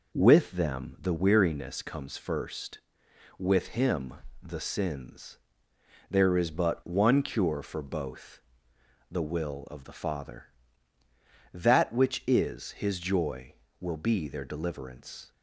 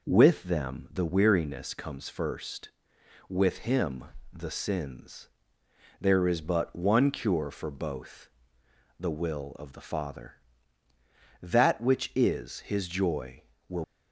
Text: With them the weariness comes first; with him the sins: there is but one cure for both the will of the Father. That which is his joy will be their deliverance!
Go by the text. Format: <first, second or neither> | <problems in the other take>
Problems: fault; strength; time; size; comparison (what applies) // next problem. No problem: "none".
first | pauses between "him" and "the"; slight; at 4.0 s; 0.26 s long; slight in the first // pauses between "both" and "the"; noticeable; at 8.2 s; 0.70 s long; noticeable in the first // stops before "be their deliverance"; at 13.8 s